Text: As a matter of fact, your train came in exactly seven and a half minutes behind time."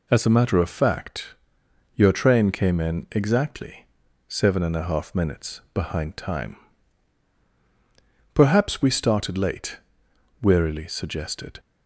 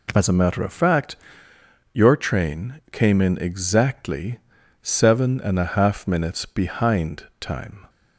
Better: second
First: pauses between "exactly" and "seven"; at 3.8 s; 0.42 s long // goes on to say "Perhaps we started late wearily suggested"; strong; from 8.3 s on; 3.2 s long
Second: pauses between "exactly" and "seven"; at 4.3 s; 0.42 s long

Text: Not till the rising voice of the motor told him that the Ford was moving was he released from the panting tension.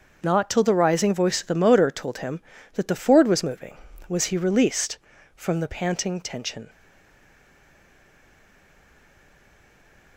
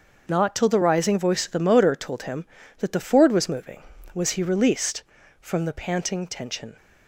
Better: second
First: starts louder than the rest; until 1.2 s; 6.5 dB // stays silent after the last word; strong; from 6.6 s on; 3.5 s long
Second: starts louder than the rest; until 1.3 s; 6.5 dB

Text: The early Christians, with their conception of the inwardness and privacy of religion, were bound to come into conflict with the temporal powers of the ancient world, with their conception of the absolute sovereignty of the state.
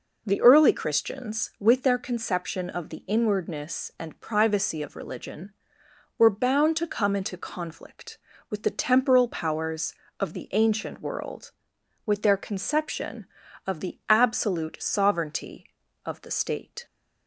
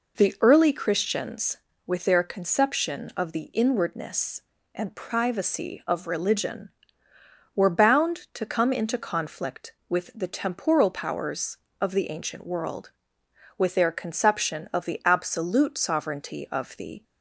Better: first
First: none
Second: stops before "state"; at 17.0 s

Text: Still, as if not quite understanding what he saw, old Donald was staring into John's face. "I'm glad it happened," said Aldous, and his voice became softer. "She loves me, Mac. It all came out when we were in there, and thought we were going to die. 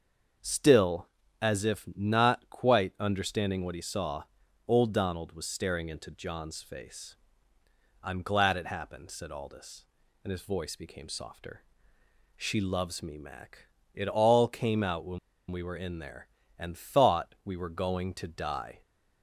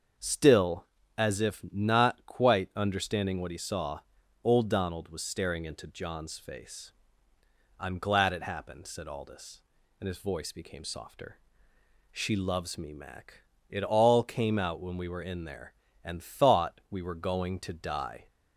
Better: second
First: starts louder than the rest; until 1.7 s; 6.5 dB // pauses between "when" and "we"; slight; at 15.1 s; 0.32 s long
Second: starts louder than the rest; until 1.5 s; 6.5 dB

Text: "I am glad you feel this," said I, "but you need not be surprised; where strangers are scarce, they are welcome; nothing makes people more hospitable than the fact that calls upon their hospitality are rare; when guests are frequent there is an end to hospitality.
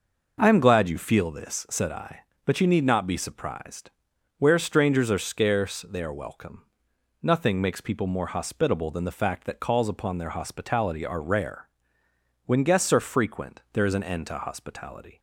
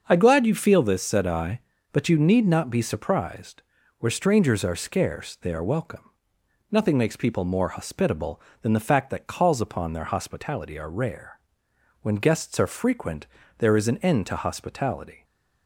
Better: first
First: none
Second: starts louder than the rest; until 1.0 s; 6.5 dB // skips "am"; at 0.1 s // pauses between "frequent" and "there"; slight; at 13.2 s; 0.32 s long

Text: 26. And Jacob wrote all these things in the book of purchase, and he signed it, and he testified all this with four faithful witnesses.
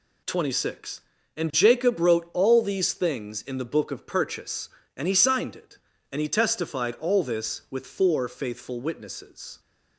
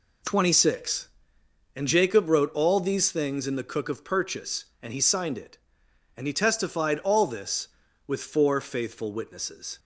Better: first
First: none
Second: says "cook" for "book"; at 3.6 s

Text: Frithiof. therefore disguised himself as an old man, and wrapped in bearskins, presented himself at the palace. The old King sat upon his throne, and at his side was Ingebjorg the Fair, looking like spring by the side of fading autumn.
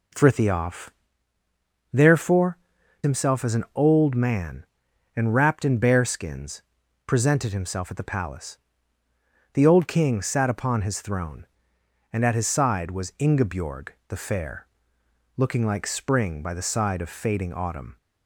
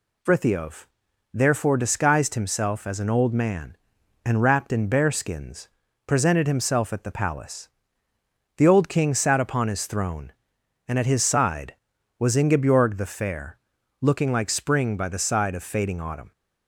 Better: second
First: skips "disguised"; at 2.8 s // pauses between "Ingebjorg" and "the"; slight; at 13.8 s; 0.20 s long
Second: none

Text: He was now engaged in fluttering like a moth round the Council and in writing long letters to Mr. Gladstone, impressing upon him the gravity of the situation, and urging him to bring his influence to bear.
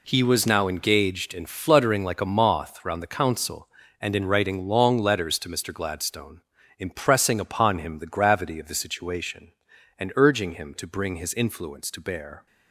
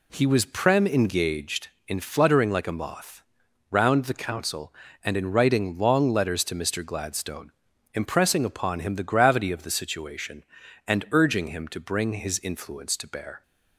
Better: first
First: none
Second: says "prem" for "now"; at 0.4 s // pauses between "moth" and "round"; noticeable; at 3.2 s; 0.48 s long

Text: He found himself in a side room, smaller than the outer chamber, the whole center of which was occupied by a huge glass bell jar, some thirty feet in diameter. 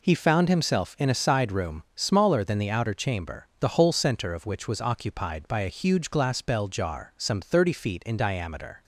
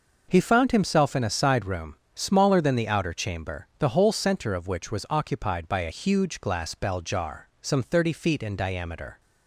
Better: neither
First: none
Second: none

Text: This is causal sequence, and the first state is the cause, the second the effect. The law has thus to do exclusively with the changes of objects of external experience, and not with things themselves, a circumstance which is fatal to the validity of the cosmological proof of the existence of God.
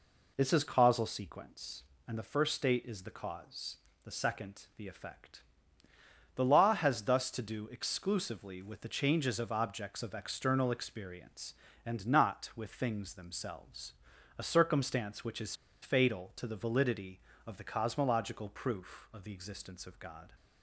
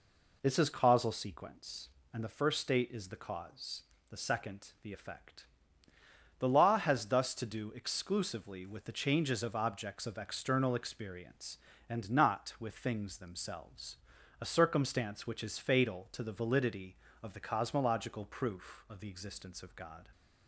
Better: second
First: pauses between "is" and "fatal"; slight; at 15.5 s; 0.28 s long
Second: none

